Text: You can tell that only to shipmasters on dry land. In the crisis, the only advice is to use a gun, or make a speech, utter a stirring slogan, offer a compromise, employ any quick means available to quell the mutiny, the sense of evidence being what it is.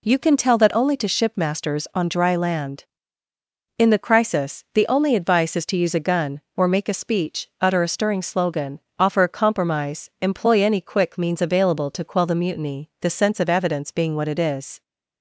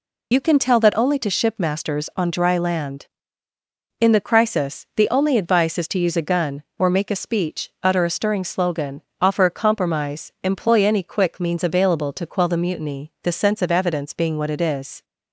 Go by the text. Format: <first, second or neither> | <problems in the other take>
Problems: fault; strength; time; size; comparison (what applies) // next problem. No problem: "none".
first | loses the start of "You"; at 0.3 s; 45 ms